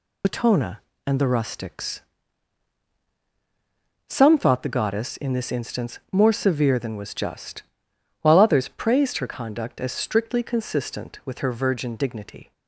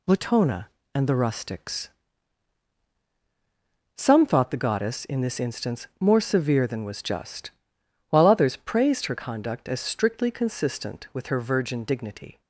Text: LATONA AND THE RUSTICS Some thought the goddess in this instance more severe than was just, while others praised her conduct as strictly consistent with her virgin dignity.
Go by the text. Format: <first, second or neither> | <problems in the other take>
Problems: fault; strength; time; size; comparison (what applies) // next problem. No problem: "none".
second | loses the start of "LATONA"; at 0.2 s; 80 ms // pauses between "RUSTICS" and "Some"; strong; at 1.9 s; 2.0 s long; strong in the second